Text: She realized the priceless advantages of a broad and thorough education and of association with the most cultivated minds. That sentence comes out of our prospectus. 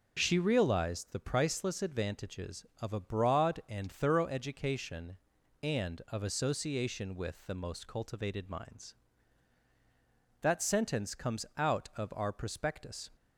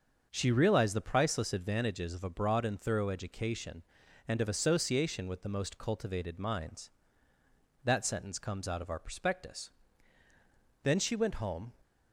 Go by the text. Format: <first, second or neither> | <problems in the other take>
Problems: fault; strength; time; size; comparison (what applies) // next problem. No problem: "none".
first | starts louder than the rest; until 1.3 s; 6.5 dB // goes on to say "Then she went home"; noticeable; from 10.8 s on; 0.88 s long